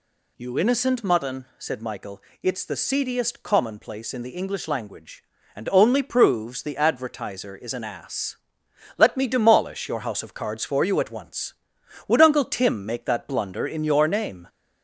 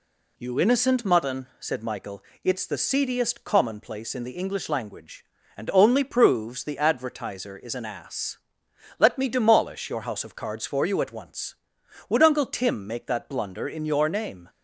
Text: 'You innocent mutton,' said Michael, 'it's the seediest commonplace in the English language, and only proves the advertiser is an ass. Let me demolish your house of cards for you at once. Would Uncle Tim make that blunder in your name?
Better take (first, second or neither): second